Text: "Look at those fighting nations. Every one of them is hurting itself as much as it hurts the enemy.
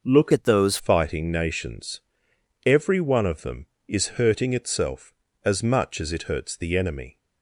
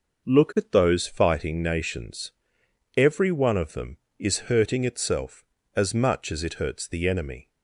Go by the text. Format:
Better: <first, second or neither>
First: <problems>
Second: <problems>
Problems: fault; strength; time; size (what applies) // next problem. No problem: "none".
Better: second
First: changes voice from "at" to "those"; from 0.3 to 0.7 s; 0.4 s long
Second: none